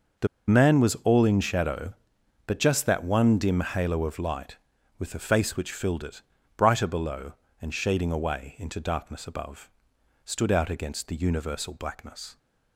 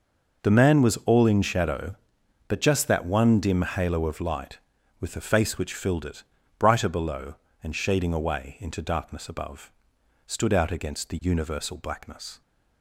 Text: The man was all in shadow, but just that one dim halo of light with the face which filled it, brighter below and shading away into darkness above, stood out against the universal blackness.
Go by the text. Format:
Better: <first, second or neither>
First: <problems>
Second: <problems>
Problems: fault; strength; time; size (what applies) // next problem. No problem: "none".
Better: second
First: pauses between "The" and "man"; slight; at 0.2 s; 0.20 s long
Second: none